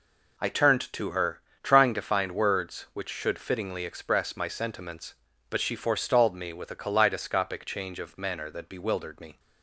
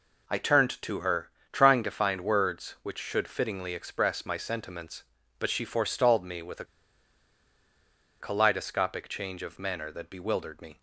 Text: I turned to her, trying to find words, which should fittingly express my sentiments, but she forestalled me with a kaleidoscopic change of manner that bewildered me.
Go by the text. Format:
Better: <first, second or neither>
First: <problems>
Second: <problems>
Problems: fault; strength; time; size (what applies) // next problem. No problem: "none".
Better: first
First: none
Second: pauses between "a" and "kaleidoscopic"; strong; at 6.6 s; 1.5 s long